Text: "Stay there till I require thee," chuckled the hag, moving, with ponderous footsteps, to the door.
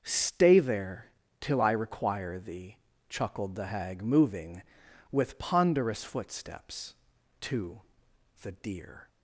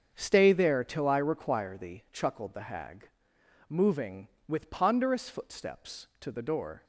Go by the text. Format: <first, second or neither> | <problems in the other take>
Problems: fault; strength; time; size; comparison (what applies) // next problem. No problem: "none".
second | starts louder than the rest; until 1.0 s; 6.5 dB; also in the second // pauses between "there" and "till"; slight; at 1.1 s; 0.30 s long // pauses between "to" and "the"; noticeable; at 7.8 s; 0.60 s long // says "deer" for "door"; at 8.5 s